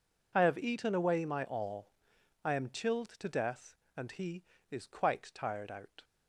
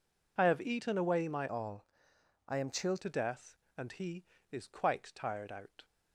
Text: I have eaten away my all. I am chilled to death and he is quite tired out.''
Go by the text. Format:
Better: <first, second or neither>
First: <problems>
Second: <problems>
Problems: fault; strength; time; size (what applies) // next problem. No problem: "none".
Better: first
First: none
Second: changes voice from "all" to "chilled"; from 1.4 to 3.0 s; 1.6 s long